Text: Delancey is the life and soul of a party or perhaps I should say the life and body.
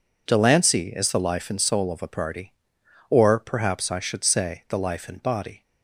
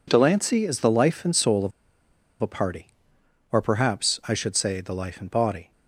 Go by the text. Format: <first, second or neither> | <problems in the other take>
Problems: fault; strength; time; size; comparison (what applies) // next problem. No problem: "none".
first | pauses between "of" and "a"; noticeable; at 1.7 s; 0.72 s long